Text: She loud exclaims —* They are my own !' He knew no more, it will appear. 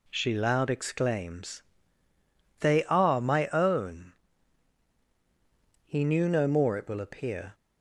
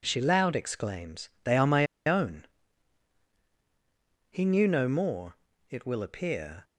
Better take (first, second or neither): first